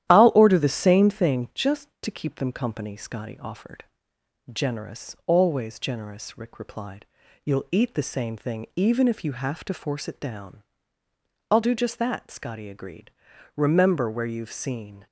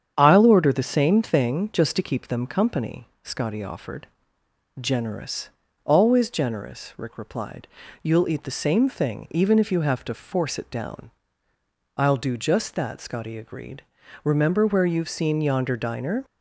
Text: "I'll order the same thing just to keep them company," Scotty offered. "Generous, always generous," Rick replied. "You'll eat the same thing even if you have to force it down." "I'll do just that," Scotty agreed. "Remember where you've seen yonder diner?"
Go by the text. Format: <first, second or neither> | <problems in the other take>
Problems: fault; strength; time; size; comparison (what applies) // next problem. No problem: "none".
second | starts louder than the rest; strong; until 1.1 s; 12 dB; strong in the second // stops before "yonder diner"; at 15.0 s